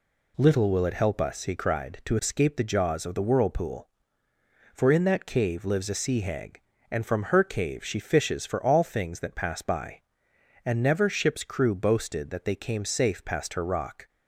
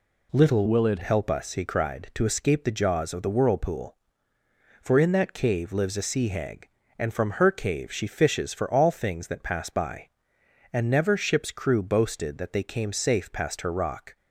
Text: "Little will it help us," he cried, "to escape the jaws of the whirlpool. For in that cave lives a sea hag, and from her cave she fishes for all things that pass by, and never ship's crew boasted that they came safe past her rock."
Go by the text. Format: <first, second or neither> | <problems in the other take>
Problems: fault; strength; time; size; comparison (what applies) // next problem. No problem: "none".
first | changes voice from "will" to "it"; from 0.6 to 0.9 s; 0.3 s long